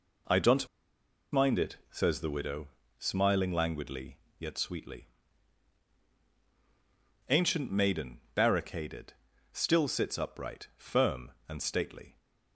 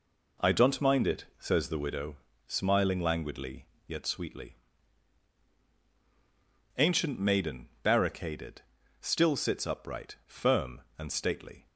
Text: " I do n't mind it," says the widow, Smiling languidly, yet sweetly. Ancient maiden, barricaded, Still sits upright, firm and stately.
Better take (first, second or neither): second